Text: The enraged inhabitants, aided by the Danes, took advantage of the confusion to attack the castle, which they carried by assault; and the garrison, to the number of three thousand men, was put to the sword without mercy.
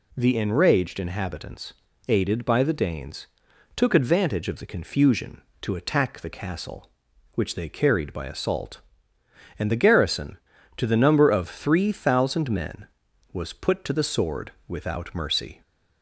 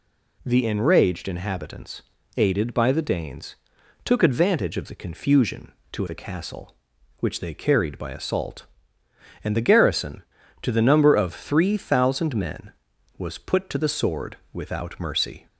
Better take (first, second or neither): first